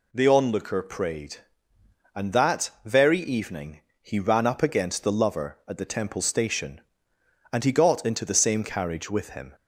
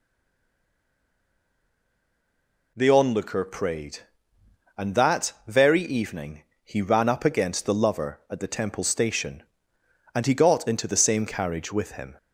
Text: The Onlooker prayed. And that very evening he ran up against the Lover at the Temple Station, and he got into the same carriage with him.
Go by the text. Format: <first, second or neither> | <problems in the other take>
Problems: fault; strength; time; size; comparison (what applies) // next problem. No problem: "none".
first | stays silent before the first word; strong; until 2.7 s; 2.7 s long // pauses between "evening" and "he"; slight; at 6.4 s; 0.20 s long; slight in the first